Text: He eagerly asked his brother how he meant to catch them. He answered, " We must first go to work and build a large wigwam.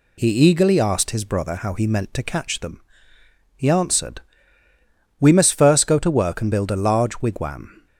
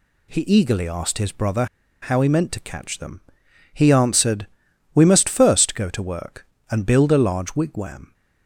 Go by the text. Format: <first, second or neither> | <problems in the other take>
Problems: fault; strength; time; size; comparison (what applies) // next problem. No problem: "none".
first | pauses between "brother" and "how"; at 1.6 s; 0.36 s long